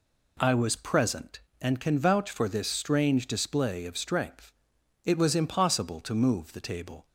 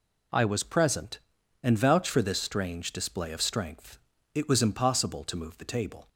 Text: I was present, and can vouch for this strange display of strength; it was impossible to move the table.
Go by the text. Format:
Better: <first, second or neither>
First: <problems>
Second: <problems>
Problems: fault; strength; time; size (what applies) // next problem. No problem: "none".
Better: first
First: none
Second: skips "can"; at 1.7 s